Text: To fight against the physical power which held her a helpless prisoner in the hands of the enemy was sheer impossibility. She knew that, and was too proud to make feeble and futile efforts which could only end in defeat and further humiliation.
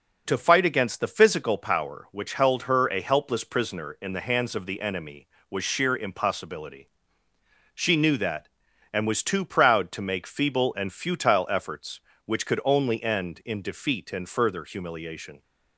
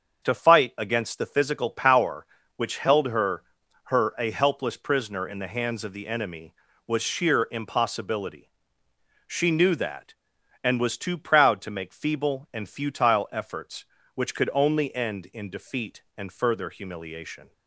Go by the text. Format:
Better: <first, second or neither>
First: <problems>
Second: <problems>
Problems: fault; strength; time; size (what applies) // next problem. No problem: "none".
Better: first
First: none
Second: starts louder than the rest; until 1.3 s; 7 dB // says "her" twice; at 3.8 s